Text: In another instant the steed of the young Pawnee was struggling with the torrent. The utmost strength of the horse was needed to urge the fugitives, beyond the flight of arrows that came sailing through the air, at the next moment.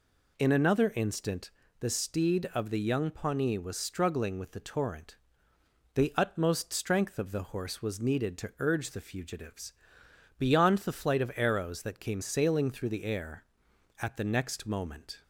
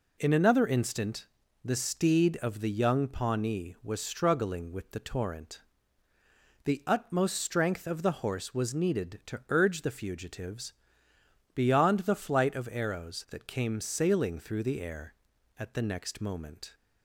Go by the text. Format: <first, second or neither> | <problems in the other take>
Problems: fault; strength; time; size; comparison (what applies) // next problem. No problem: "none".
neither | pauses between "instant" and "the"; slight; the same in both